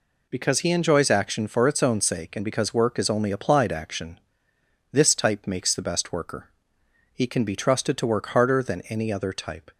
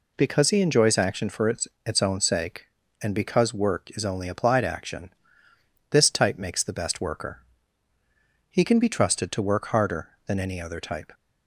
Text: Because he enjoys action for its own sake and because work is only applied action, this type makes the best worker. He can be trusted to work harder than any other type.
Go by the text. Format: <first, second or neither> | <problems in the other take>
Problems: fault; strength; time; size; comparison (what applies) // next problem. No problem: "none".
first | says "its" twice; at 1.8 s